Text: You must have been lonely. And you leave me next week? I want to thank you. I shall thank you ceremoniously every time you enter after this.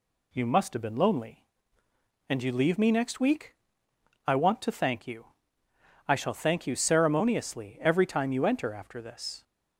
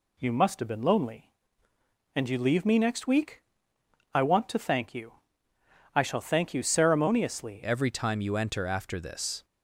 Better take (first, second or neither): first